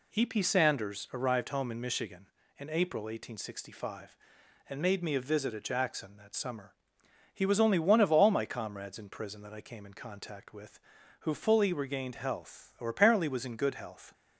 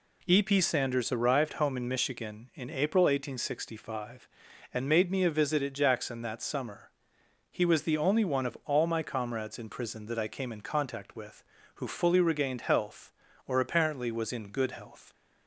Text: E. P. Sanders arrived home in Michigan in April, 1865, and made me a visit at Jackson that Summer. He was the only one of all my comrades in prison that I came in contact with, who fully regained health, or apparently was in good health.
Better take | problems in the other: second | skips "the"; at 7.6 s

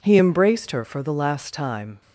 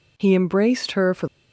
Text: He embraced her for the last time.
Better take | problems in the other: first | stops before "the last time"; at 1.2 s

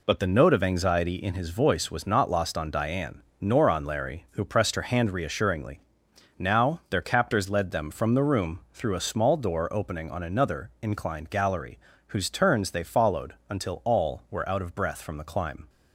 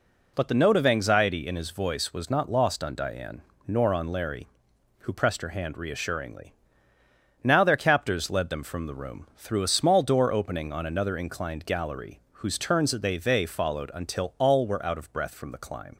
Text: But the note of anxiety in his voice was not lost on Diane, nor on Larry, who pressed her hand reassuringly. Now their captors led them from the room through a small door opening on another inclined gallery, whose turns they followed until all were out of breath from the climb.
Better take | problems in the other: first | says "they" twice; at 13.1 s

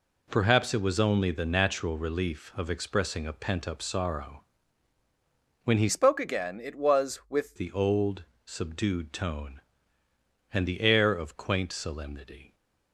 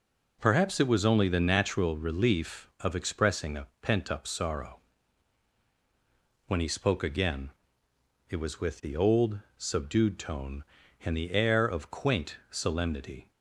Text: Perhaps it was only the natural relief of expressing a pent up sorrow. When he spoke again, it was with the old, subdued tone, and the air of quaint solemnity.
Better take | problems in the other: second | changes voice from "spoke" to "with"; from 5.8 to 7.5 s; 1.7 s long

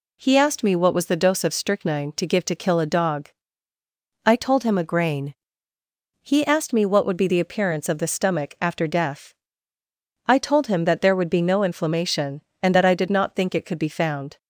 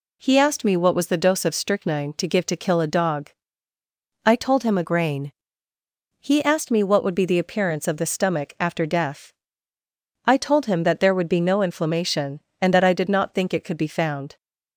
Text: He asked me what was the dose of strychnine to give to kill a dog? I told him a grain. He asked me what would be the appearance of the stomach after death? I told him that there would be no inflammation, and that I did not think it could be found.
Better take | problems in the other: neither | none

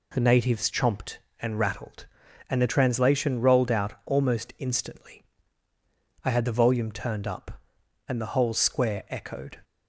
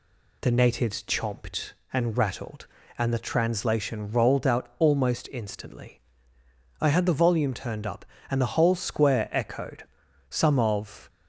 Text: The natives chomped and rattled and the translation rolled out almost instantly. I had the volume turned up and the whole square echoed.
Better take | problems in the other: first | goes on to say "Some of"; noticeable; from 10.2 s on; 0.80 s long

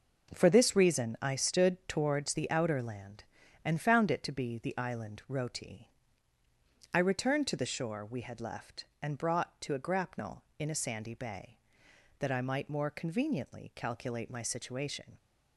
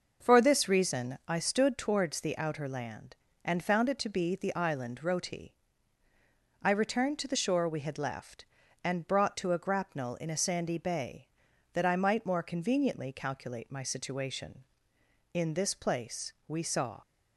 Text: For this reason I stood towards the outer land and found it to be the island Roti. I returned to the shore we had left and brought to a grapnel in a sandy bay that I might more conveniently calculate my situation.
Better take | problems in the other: first | starts louder than the rest; noticeable; until 1.3 s; 6 dB // goes on to say "In this place we saw"; strong; from 15.3 s on; 1.6 s long

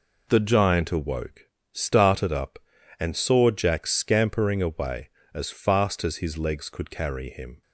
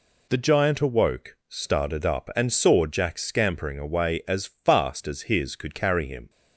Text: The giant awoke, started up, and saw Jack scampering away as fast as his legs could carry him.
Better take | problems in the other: first | skips "legs"; at 5.5 s

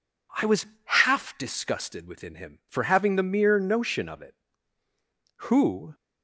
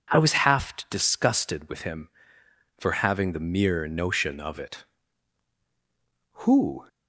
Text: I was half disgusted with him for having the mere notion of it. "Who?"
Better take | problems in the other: second | pauses between "was" and "half"; slight; at 0.6 s; 0.18 s long // says "within" for "with"; at 2.0 s

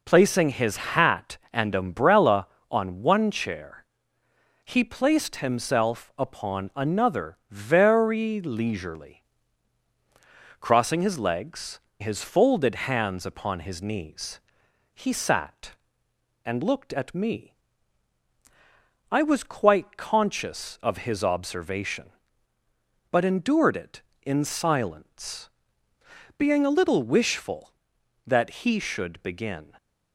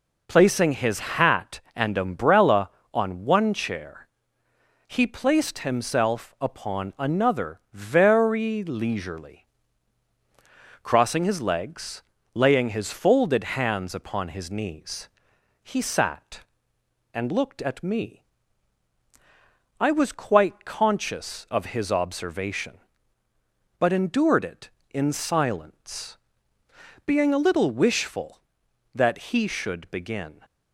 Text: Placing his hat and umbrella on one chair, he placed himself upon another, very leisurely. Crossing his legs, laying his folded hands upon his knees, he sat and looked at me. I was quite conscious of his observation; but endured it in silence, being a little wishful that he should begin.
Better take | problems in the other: second | skips "laying"; at 11.8 s

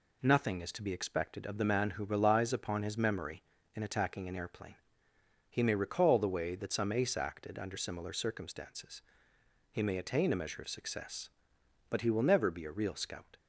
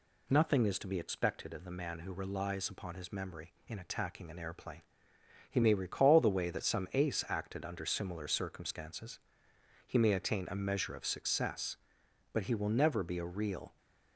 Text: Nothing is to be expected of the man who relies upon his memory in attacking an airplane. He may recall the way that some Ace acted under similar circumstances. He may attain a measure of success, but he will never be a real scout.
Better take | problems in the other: first | stops before "scout"; at 13.7 s

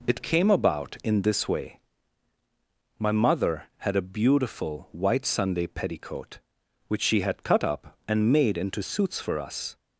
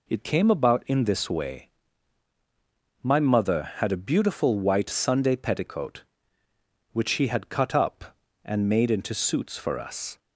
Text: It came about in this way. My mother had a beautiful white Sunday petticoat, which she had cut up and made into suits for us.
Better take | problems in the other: neither | none

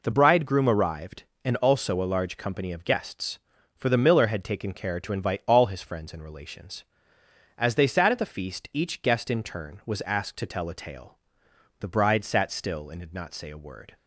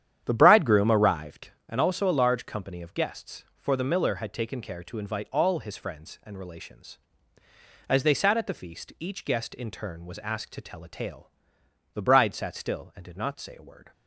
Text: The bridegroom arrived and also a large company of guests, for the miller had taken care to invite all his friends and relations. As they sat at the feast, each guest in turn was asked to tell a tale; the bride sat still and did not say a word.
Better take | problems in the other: first | starts louder than the rest; strong; until 1.5 s; 10 dB

